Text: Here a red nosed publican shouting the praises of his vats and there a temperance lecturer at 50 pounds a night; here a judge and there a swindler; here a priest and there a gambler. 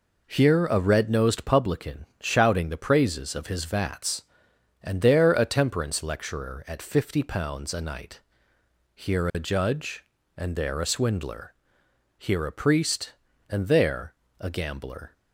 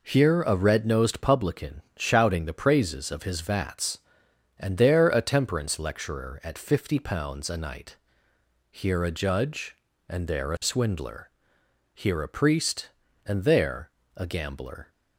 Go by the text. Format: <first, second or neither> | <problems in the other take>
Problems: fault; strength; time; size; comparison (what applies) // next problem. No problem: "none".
neither | pauses between "there" and "a"; slight; the same in both